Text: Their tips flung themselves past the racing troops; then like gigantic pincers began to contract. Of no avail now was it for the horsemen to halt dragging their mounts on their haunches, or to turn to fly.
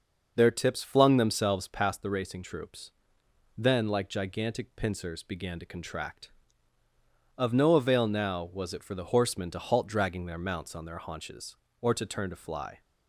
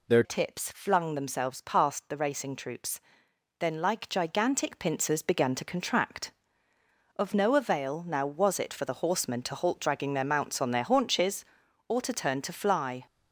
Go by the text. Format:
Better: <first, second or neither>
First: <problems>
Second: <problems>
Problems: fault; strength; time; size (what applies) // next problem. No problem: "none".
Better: first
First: none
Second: changes voice at "tips"; from 0.2 s on; 12.8 s long